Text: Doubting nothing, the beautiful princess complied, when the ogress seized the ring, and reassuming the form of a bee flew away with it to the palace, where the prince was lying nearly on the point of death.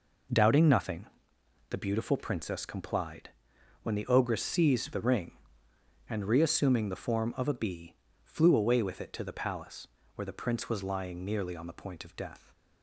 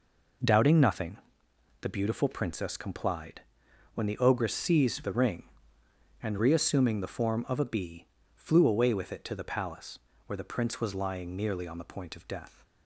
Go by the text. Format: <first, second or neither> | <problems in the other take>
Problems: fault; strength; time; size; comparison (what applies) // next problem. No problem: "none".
neither | pauses between "bee" and "flew"; slight; the same in both